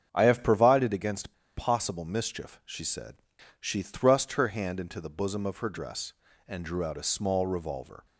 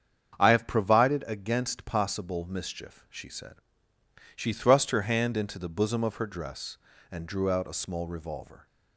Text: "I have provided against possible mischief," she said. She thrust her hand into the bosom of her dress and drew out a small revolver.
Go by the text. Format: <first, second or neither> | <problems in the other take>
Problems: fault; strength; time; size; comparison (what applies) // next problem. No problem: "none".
second | starts louder than the rest; strong; until 1.1 s; 8 dB; strong in the second // pauses between "against" and "possible"; slight; at 1.3 s; 0.22 s long